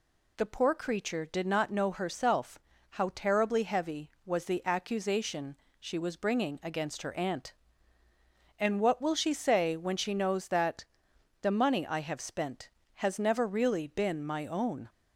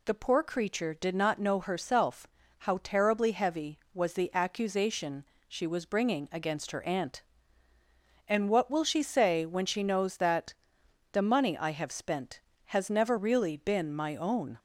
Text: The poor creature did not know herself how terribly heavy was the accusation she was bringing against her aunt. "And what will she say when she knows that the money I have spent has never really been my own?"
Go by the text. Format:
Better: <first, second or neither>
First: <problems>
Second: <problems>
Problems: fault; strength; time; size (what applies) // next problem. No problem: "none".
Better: neither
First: pauses between "herself" and "how"; slight; at 2.5 s; 0.34 s long // pauses between "accusation" and "she"; slight; at 5.5 s; 0.22 s long // pauses between "that" and "the"; noticeable; at 10.8 s; 0.56 s long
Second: pauses between "herself" and "how"; slight; at 2.2 s; 0.34 s long // pauses between "accusation" and "she"; slight; at 5.2 s; 0.22 s long // pauses between "that" and "the"; noticeable; at 10.5 s; 0.56 s long